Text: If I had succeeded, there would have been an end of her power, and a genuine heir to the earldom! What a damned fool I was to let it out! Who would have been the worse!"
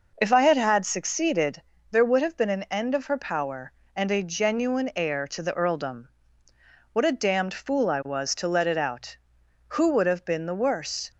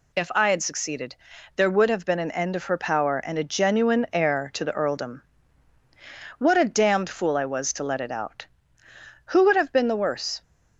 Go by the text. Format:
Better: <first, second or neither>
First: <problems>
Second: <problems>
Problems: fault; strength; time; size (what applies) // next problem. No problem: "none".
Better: second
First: says "had" twice; at 0.5 s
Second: none